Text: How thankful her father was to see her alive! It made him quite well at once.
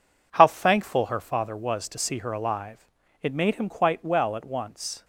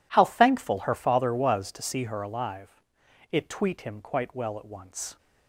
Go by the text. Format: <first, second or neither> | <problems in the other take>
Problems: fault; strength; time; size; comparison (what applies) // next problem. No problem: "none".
first | says "tweet" for "made"; at 3.4 s